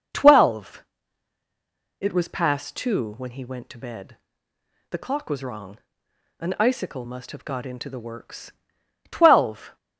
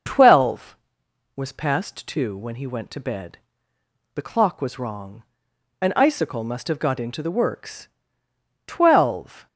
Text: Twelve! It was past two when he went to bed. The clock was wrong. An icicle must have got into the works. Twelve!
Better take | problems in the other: first | skips "It"; at 1.0 s

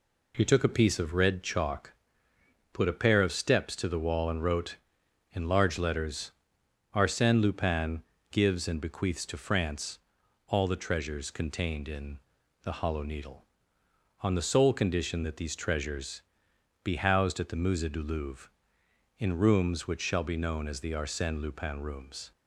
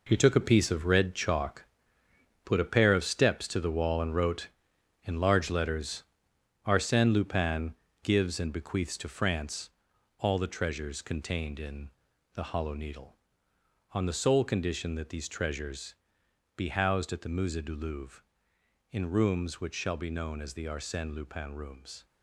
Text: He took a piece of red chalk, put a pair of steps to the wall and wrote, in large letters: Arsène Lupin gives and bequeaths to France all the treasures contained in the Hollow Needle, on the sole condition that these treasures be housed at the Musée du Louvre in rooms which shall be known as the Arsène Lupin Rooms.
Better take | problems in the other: first | gets quieter; strong; throughout; 9.5 dB // pauses between "Lupin" and "gives"; slight; at 7.7 s; 0.30 s long; slight in the first // pauses between "France" and "all"; noticeable; at 9.6 s; 0.50 s long; noticeable in the first // pauses between "in" and "the"; noticeable; at 11.8 s; 0.46 s long; noticeable in the first // pauses between "treasures" and "be"; noticeable; at 15.9 s; 0.60 s long; noticeable in the first

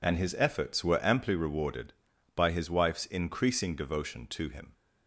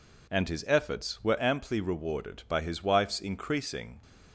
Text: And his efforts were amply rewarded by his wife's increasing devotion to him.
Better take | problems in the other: first | stops before "devotion to him"; at 4.0 s

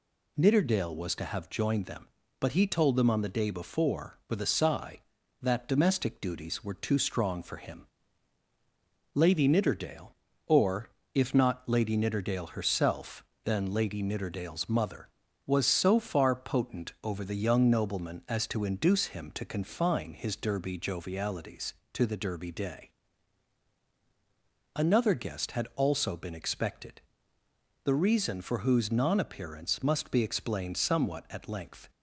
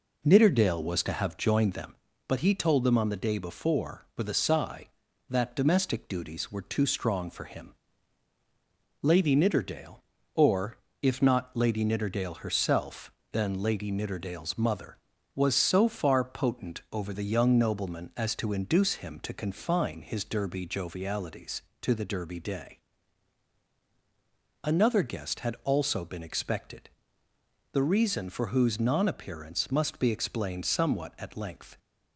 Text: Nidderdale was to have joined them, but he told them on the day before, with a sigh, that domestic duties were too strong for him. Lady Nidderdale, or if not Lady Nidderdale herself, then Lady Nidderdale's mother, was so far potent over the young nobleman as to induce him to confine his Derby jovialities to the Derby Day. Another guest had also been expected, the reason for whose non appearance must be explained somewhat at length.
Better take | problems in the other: first | starts louder than the rest; noticeable; until 1.9 s; 4 dB // pauses between "or" and "if"; slight; at 10.7 s; 0.26 s long; slight in the first

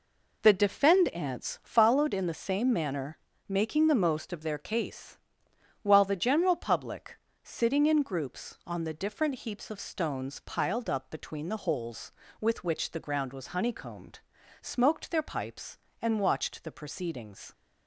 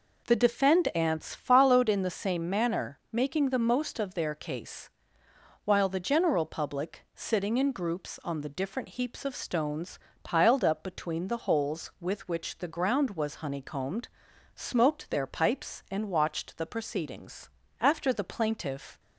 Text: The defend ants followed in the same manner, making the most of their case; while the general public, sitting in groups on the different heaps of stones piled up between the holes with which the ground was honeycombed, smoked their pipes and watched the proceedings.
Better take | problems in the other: first | pauses between "stones" and "piled"; slight; at 9.9 s; 0.24 s long // goes on to say "After the plaintiff"; noticeable; from 17.7 s on; 1.2 s long

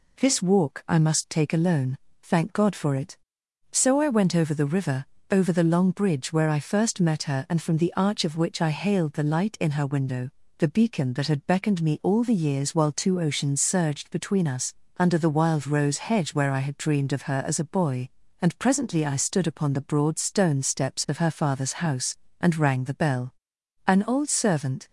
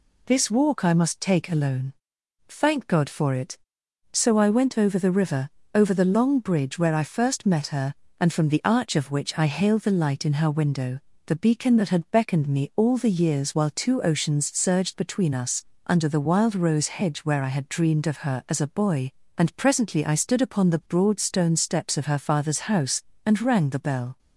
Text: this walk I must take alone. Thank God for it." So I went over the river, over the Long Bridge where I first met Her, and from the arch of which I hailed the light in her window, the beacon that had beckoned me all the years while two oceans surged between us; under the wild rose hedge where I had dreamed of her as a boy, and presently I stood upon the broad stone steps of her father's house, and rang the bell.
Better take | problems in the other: second | goes on to say "An old servant"; noticeable; from 23.8 s on; 1.0 s long

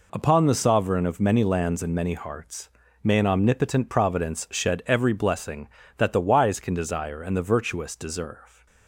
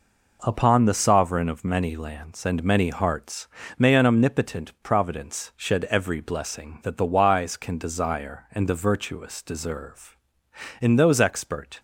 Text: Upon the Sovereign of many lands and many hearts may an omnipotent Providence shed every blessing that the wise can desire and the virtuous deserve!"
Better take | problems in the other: first | pauses between "hearts" and "may"; slight; at 3.4 s; 0.30 s long; slight in the first // goes on to say "In those expert"; noticeable; from 10.8 s on; 0.98 s long

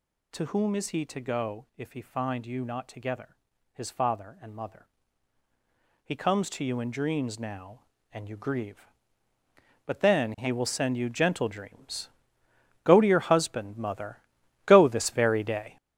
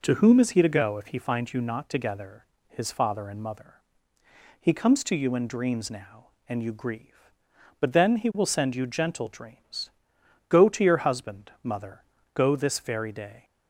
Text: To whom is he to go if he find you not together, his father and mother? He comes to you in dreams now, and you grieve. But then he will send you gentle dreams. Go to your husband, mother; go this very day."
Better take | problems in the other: second | gets louder; strong; throughout; 8 dB

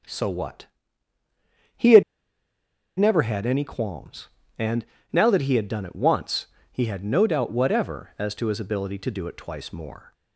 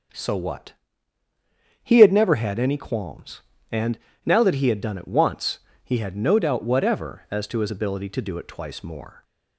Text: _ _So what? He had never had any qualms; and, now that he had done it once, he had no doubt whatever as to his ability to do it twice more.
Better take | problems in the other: second | starts louder than the rest; until 3.1 s; 6.5 dB; also in the second // pauses between "had" and "never"; noticeable; at 2.0 s; 0.95 s long

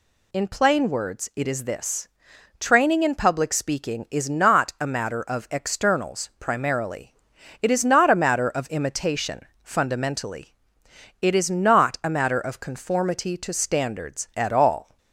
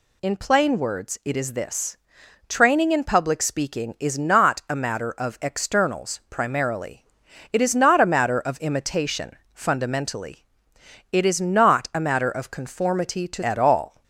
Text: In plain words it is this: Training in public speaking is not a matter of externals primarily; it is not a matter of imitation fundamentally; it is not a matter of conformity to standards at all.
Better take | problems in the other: first | pauses between "imitation" and "fundamentally"; slight; at 9.3 s; 0.20 s long; slight in the first // skips "standards"; at 13.4 s

